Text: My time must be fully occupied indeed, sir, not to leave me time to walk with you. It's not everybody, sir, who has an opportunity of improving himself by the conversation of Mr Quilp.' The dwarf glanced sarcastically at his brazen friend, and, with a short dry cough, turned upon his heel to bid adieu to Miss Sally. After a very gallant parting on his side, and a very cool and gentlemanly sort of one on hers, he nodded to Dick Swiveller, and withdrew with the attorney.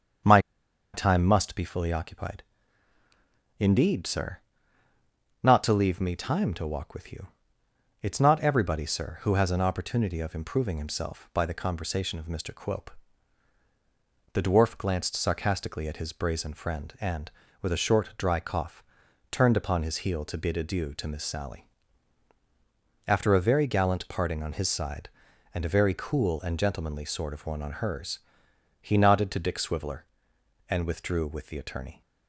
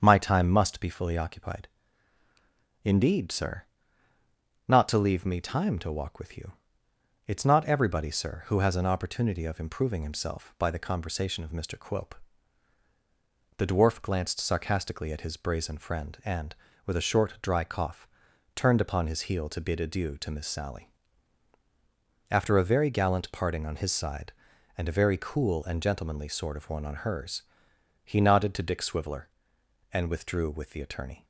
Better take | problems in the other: second | starts louder than the rest; strong; until 1.8 s; 7.5 dB; strong in the second // pauses between "My" and "time"; noticeable; at 0.3 s; 0.54 s long // pauses between "occupied" and "indeed"; at 2.4 s; 1.1 s long; also in the second

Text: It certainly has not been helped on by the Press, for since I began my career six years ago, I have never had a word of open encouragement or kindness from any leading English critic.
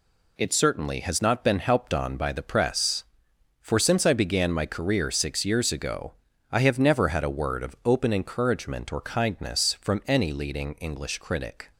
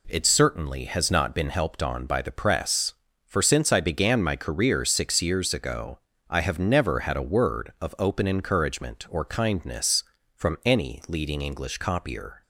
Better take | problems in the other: first | says "copier" for "critic"; at 11.7 s

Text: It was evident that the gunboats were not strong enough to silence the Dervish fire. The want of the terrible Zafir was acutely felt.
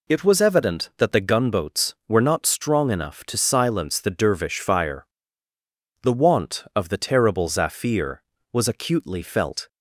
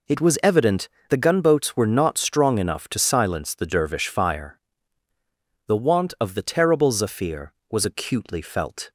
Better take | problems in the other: first | skips "that"; at 0.9 s

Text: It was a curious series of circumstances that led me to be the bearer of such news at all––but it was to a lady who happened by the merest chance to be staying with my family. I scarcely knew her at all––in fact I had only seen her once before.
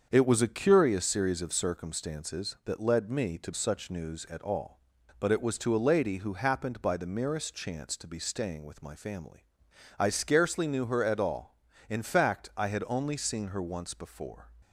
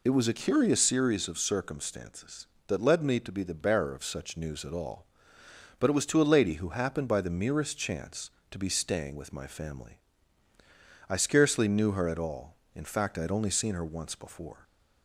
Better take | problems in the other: second | starts louder than the rest; until 1.1 s; 7 dB // skips "be the bearer of"; at 3.5 s

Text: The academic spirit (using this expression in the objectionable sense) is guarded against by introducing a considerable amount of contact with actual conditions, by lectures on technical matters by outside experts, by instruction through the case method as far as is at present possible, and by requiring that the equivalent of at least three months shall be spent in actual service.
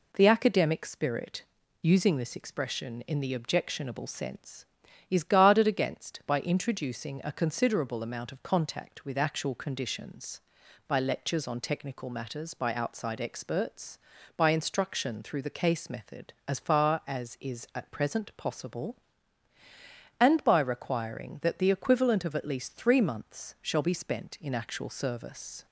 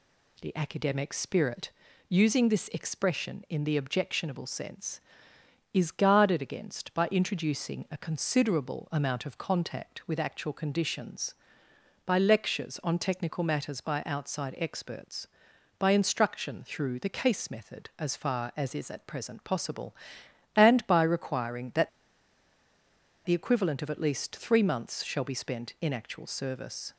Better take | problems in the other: first | pauses between "that" and "the"; strong; at 21.8 s; 1.3 s long

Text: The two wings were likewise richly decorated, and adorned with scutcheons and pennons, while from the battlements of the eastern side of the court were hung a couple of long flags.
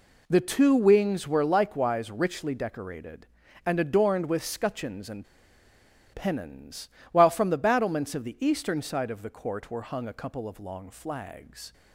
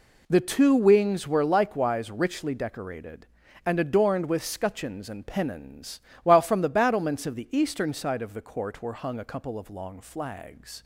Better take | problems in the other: second | pauses between "and" and "pennons"; noticeable; at 5.2 s; 0.89 s long

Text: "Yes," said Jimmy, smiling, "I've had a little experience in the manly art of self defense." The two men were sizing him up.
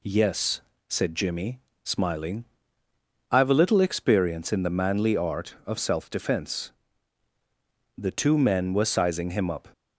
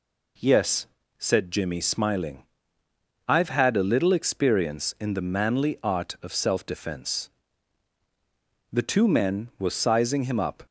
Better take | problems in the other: second | skips "had"; at 3.4 s

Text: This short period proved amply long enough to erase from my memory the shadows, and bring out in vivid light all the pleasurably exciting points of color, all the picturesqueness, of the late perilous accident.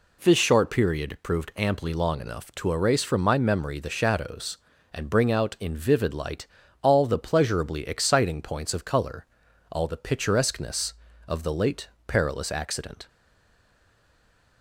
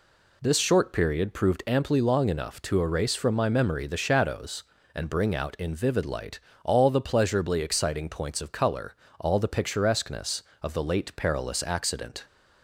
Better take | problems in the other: second | pauses between "light" and "all"; slight; at 6.4 s; 0.36 s long; slight in the second // pauses between "late" and "perilous"; slight; at 11.8 s; 0.18 s long // stays silent after the last word; noticeable; from 13.0 s on; 1.6 s long

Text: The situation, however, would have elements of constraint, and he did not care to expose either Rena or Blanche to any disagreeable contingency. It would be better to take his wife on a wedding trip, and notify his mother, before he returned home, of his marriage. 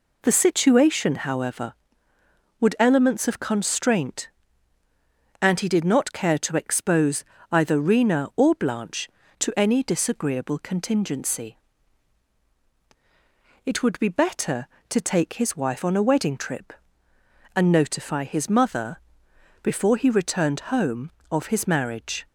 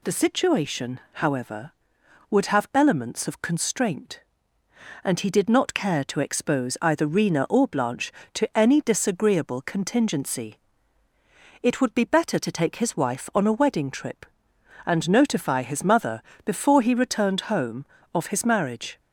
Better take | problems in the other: second | skips "have"; at 2.7 s // pauses between "expose" and "either"; slight; at 7.2 s; 0.28 s long

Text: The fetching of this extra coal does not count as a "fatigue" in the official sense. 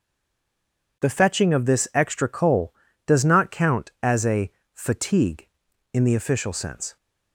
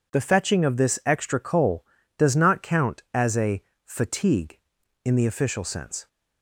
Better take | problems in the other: second | stays silent before the first word; until 1.0 s; 1.0 s long // pauses between "a" and "fatigue"; slight; at 4.5 s; 0.24 s long; slight in the second

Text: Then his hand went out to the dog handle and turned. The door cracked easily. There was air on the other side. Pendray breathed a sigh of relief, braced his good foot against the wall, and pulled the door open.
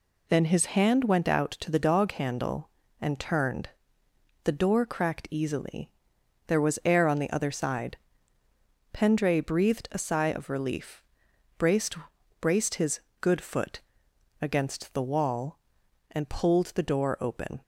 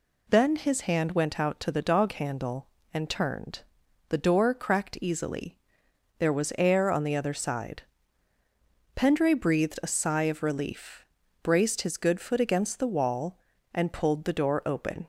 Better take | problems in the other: second | says "braced" twice; at 12.4 s // pauses between "his" and "good"; slight; at 12.9 s; 0.22 s long // pauses between "foot" and "against"; noticeable; at 13.8 s; 0.60 s long

